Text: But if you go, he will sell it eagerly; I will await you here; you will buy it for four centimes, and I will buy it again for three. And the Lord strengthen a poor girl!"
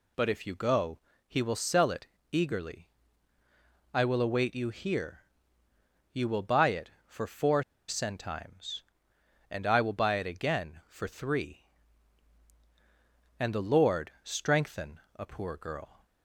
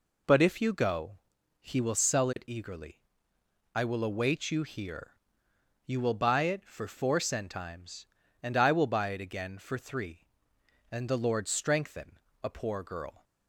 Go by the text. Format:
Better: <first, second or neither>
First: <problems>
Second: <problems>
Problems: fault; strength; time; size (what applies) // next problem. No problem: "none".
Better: second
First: pauses between "it" and "eagerly"; slight; at 2.0 s; 0.24 s long // pauses between "four" and "centimes"; slight; at 7.6 s; 0.25 s long // pauses between "strengthen" and "a"; slight; at 15.0 s; 0.16 s long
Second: pauses between "strengthen" and "a"; slight; at 12.1 s; 0.26 s long